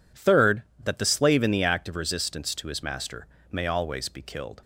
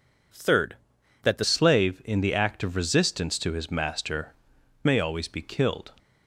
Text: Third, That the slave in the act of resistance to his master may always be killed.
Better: first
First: pauses between "master" and "may"; slight; at 3.2 s; 0.22 s long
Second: changes voice at "slave"; from 1.4 s on; 4.5 s long // pauses between "master" and "may"; noticeable; at 4.3 s; 0.48 s long

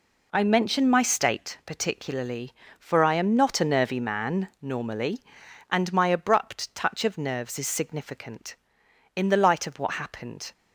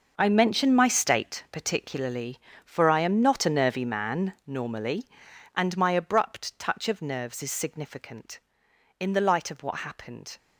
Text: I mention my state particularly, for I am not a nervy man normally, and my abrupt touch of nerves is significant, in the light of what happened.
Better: first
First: none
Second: gets quieter; strong; throughout; 12.5 dB

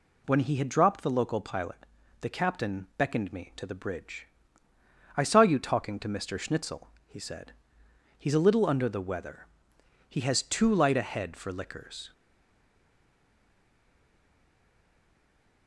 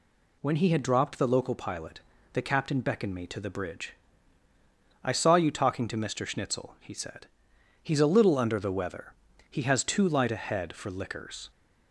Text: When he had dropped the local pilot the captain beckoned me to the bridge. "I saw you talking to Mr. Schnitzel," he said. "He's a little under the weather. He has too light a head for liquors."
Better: second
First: pauses between "pilot" and "the"; at 1.8 s; 0.38 s long // stays silent after the last word; strong; from 12.1 s on; 3.5 s long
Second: pauses between "pilot" and "the"; slight; at 2.0 s; 0.32 s long

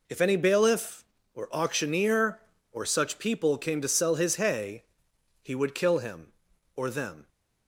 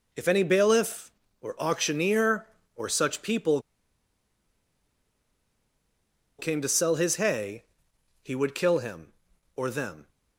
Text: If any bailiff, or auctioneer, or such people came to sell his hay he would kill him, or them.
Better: first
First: pauses between "hay" and "he"; noticeable; at 4.8 s; 0.58 s long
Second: pauses between "people" and "came"; strong; at 3.5 s; 2.7 s long // pauses between "hay" and "he"; noticeable; at 7.6 s; 0.58 s long

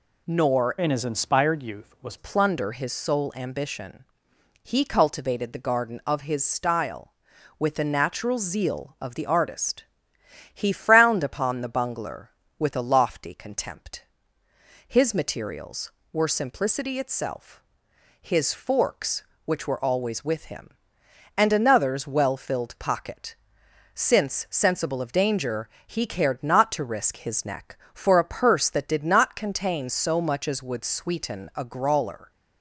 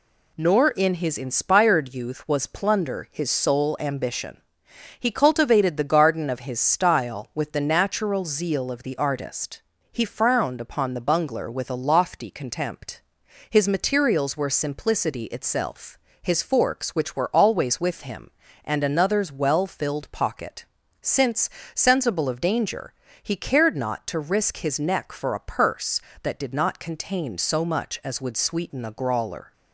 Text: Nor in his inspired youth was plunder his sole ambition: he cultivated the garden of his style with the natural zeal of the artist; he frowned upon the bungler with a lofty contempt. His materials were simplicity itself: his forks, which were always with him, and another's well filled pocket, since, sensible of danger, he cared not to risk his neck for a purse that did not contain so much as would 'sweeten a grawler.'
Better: second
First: changes voice from "in" to "was"; from 0.7 to 2.1 s; 1.4 s long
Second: none

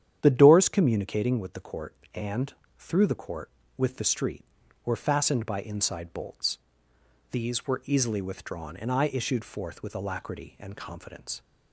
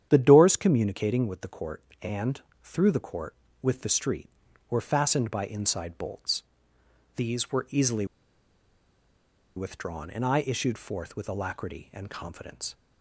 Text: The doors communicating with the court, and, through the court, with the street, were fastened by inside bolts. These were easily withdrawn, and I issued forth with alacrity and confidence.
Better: first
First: starts louder than the rest; strong; until 1.2 s; 9.5 dB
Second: starts louder than the rest; strong; until 1.1 s; 9.5 dB // pauses between "easily" and "withdrawn"; strong; at 8.0 s; 1.5 s long

